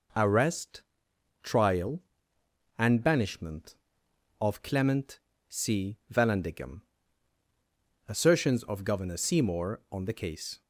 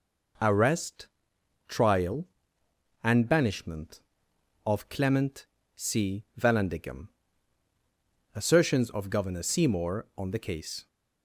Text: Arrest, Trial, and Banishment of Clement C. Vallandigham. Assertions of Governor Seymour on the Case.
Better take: neither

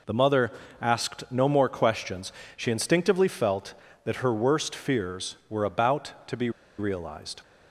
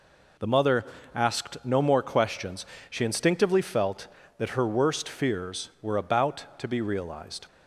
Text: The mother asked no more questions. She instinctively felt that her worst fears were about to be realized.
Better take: second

